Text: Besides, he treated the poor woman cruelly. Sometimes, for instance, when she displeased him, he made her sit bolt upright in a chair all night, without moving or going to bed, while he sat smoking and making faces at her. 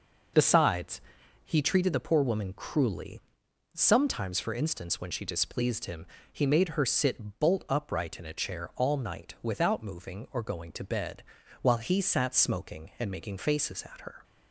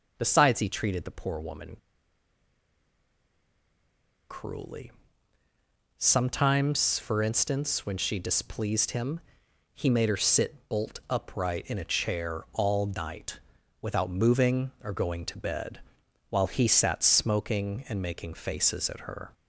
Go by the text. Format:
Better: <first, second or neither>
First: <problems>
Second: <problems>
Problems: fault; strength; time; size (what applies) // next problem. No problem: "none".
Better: first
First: none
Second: pauses between "woman" and "cruelly"; strong; at 1.7 s; 2.5 s long